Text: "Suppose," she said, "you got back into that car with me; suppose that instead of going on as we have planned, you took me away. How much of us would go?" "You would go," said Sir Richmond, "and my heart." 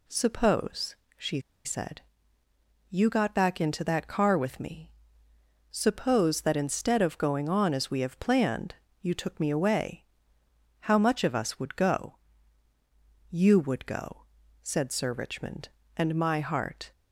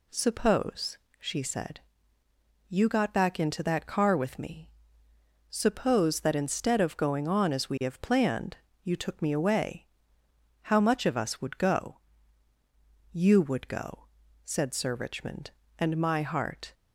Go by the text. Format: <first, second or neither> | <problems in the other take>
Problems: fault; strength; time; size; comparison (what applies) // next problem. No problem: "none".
second | pauses between "she" and "said"; slight; at 1.3 s; 0.25 s long